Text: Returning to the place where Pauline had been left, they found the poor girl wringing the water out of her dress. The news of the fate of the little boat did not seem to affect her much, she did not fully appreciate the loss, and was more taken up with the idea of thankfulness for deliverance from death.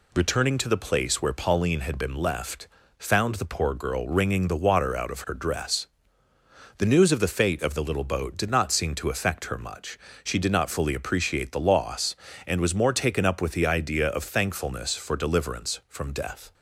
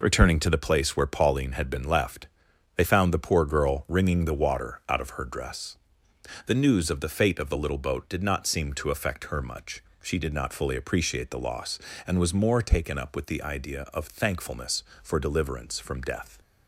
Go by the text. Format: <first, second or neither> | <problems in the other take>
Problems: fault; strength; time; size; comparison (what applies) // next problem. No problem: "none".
second | skips "they"; at 2.8 s